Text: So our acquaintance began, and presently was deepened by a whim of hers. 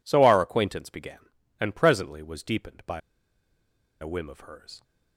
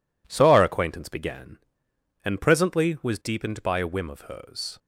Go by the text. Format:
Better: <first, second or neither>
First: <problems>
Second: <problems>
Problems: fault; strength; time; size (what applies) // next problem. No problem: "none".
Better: second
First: pauses between "by" and "a"; at 3.0 s; 1.0 s long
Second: none